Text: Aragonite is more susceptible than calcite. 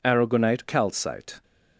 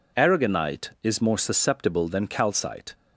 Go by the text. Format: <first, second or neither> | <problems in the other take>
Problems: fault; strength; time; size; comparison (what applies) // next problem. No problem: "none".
second | skips "is more susceptible than"; at 0.6 s